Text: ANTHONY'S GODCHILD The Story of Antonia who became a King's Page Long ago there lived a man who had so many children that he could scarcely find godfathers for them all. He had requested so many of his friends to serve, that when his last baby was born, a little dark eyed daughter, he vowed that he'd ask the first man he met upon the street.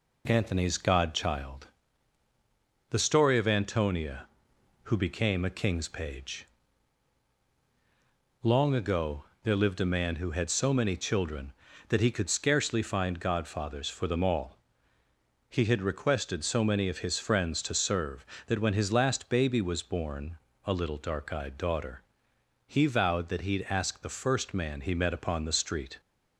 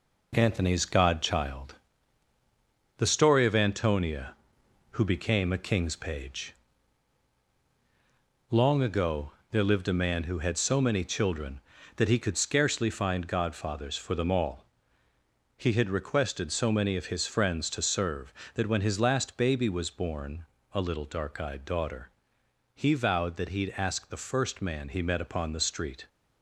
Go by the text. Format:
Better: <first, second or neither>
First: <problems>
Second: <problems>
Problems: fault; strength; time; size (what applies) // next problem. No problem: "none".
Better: first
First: pauses between "GODCHILD" and "The"; at 1.6 s; 1.2 s long // pauses between "Page" and "Long"; strong; at 6.4 s; 1.9 s long // pauses between "ago" and "there"; slight; at 9.2 s; 0.22 s long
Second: gets quieter; noticeable; throughout; 6 dB // pauses between "GODCHILD" and "The"; at 1.7 s; 1.2 s long // pauses between "Page" and "Long"; strong; at 6.5 s; 1.9 s long // pauses between "ago" and "there"; slight; at 9.2 s; 0.22 s long